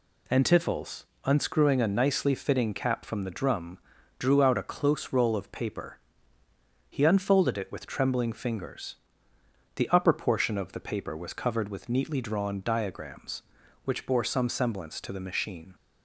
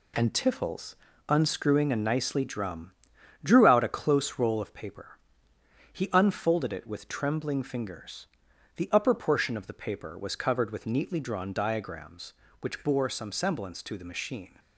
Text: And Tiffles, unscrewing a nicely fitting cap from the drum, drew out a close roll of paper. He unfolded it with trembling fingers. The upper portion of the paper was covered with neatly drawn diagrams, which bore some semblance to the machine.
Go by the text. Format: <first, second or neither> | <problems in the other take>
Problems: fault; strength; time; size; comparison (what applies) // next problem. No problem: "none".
first | skips "fitting cap from the"; at 2.4 s